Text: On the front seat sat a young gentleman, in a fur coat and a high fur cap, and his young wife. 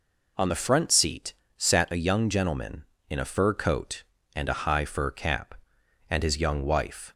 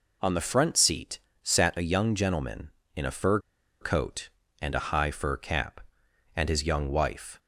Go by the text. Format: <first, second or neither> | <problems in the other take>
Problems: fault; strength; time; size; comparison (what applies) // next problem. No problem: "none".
first | pauses between "seat" and "sat"; slight; at 1.1 s; 0.24 s long; slight in the first // pauses between "fur" and "coat"; at 3.3 s; 0.42 s long